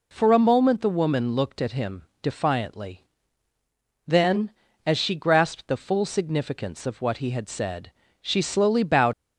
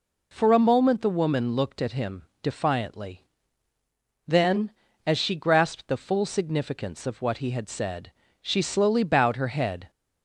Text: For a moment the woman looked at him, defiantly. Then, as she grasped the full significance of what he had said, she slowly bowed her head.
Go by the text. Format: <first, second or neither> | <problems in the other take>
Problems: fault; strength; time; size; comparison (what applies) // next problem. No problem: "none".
second | stops before "her head"; at 9.1 s